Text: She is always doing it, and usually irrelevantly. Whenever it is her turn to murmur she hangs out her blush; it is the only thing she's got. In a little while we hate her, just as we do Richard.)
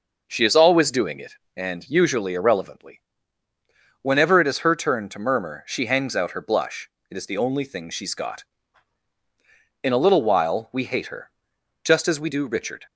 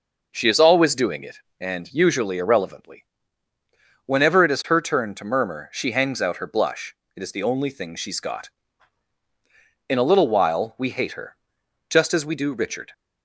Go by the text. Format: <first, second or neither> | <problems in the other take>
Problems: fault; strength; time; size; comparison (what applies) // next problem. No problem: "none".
neither | none